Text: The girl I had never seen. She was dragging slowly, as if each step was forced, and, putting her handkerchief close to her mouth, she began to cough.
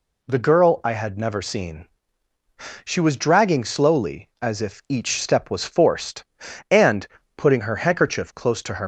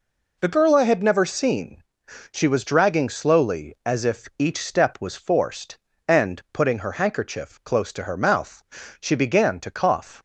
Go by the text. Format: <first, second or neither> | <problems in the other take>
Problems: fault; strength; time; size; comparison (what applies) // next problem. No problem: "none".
second | stops before "mouth she began to cough"; at 8.8 s